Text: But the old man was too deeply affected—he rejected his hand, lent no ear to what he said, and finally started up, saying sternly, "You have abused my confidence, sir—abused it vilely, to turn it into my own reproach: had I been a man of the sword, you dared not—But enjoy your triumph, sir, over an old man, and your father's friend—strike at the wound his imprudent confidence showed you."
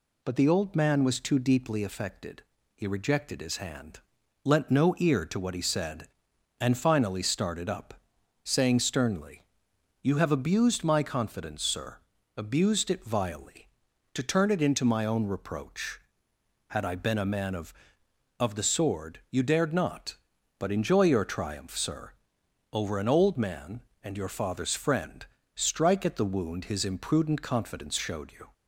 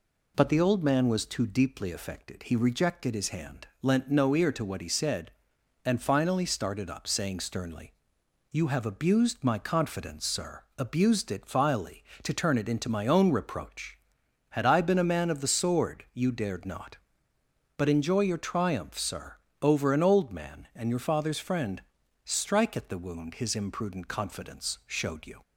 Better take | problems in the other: second | says "of" twice; at 18.3 s

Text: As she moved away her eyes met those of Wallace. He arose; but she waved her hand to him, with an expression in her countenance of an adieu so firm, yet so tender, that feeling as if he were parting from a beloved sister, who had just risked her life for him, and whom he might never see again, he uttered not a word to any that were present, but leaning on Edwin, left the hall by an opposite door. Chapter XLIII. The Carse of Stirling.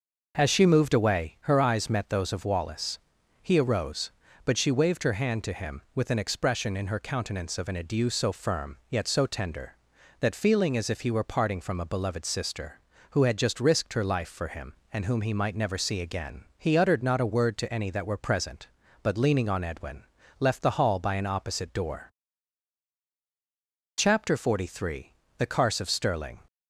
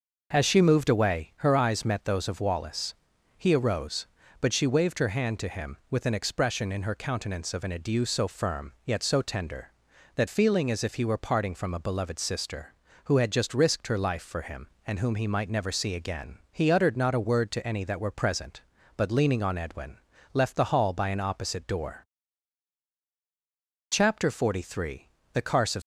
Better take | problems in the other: first | stops before "Stirling"; at 25.8 s

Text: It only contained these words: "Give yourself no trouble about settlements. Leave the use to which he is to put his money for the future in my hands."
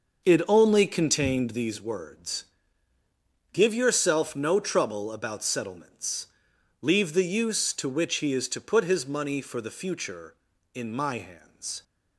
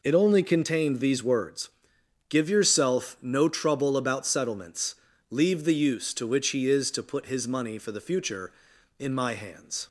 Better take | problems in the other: second | starts louder than the rest; noticeable; until 1.8 s; 6 dB

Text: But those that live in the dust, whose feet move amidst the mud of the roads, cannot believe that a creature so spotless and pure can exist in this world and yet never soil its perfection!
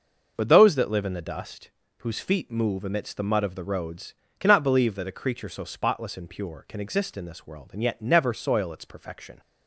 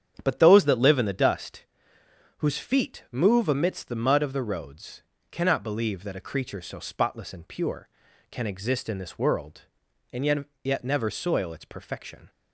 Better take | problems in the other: first | starts louder than the rest; strong; until 1.2 s; 8.5 dB // says "yet" twice; at 10.6 s

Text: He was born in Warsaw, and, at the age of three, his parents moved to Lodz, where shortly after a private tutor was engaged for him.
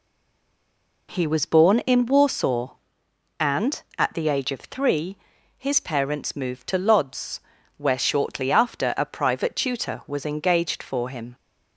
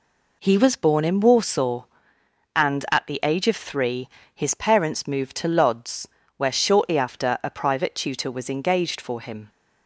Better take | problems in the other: second | stays silent before the first word; until 1.0 s; 1.0 s long

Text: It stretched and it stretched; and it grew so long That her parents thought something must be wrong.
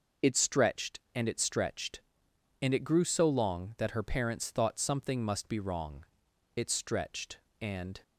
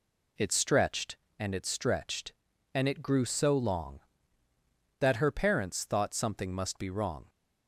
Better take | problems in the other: second | goes on to say "It stretched and"; from 6.5 s on; 1.4 s long

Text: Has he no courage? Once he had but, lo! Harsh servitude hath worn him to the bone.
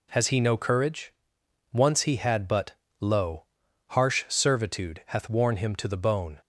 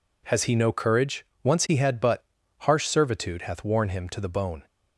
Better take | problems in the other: first | skips "lo"; at 2.4 s

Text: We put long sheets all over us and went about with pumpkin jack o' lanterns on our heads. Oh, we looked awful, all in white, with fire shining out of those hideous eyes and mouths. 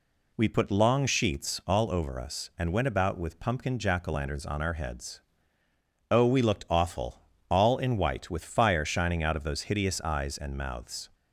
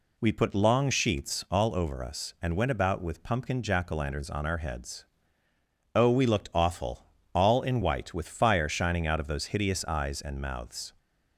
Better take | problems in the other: neither | none

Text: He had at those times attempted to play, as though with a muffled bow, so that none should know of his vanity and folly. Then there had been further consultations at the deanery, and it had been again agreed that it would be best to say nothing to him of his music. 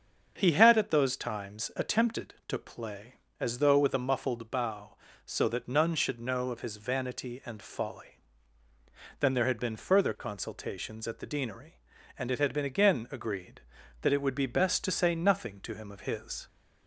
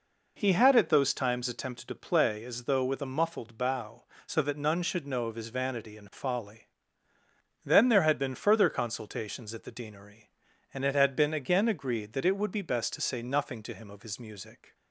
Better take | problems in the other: second | starts louder than the rest; until 1.3 s; 7 dB // stops before "music"; at 16.4 s

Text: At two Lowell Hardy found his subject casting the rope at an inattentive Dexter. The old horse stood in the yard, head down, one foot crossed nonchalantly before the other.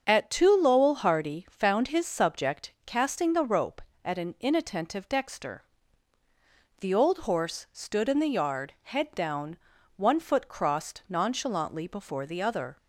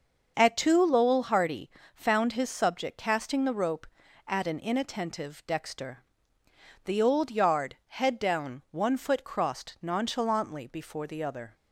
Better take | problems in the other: first | starts louder than the rest; until 1.3 s; 6.5 dB; also in the first // pauses between "Hardy" and "found"; slight; at 1.6 s; 0.26 s long // skips "horse stood in the"; at 7.3 s

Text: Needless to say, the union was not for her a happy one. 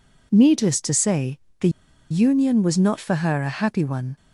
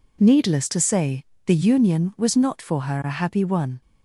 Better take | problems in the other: second | pauses between "the" and "union"; at 1.6 s; 0.41 s long

